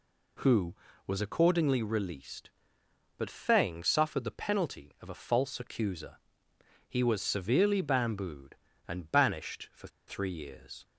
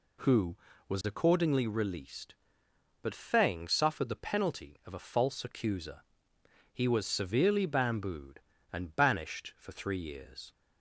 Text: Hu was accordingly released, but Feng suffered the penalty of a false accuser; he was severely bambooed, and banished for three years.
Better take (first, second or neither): second